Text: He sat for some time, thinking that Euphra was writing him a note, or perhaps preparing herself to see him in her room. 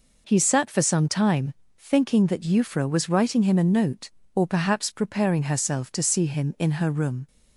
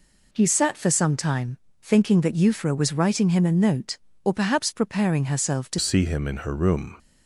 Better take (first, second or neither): first